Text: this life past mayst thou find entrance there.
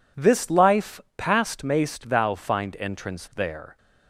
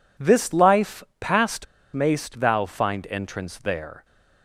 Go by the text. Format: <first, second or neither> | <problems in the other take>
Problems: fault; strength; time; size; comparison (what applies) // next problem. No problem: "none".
first | pauses between "life" and "past"; slight; at 1.0 s; 0.16 s long; slight in the first // pauses between "past" and "mayst"; slight; at 1.6 s; 0.29 s long